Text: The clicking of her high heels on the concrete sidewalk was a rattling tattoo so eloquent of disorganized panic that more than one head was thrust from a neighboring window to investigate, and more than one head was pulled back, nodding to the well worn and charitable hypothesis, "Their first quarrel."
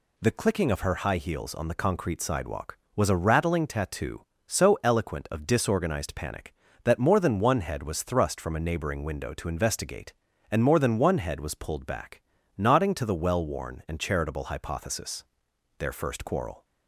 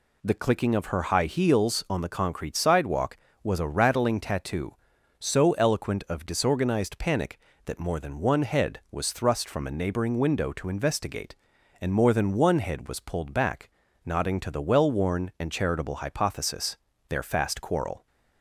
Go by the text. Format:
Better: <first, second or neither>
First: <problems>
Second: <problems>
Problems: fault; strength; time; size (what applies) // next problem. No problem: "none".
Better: first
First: none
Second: says "fast" for "first"; at 17.2 s